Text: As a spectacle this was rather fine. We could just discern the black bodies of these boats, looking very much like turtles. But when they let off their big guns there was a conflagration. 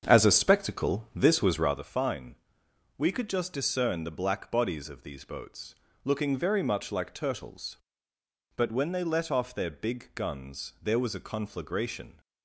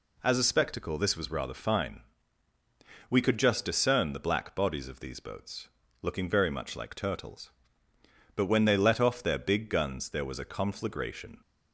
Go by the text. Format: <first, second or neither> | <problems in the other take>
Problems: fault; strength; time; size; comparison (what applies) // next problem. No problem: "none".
second | starts louder than the rest; strong; until 1.8 s; 7.5 dB